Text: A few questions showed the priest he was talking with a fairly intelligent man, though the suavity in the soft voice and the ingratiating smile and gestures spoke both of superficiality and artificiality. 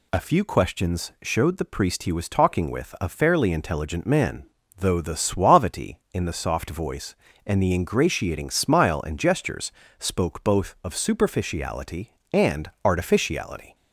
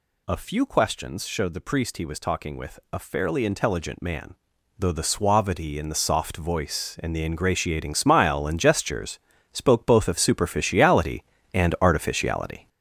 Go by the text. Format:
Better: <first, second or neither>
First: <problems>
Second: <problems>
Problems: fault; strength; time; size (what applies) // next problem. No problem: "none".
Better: first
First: pauses between "gestures" and "spoke"; slight; at 9.7 s; 0.28 s long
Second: gets louder; throughout; 6.5 dB // pauses between "gestures" and "spoke"; slight; at 9.1 s; 0.34 s long